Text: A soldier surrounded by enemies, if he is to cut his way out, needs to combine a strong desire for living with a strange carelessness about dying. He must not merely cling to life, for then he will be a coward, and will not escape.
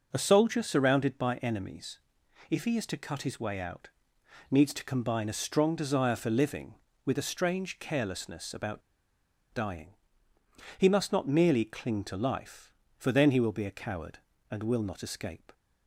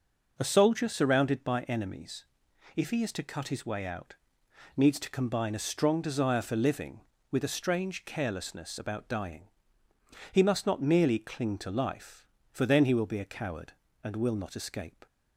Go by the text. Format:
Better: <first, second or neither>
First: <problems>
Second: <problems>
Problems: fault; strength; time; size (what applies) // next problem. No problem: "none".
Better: second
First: pauses between "about" and "dying"; noticeable; at 8.8 s; 0.71 s long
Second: none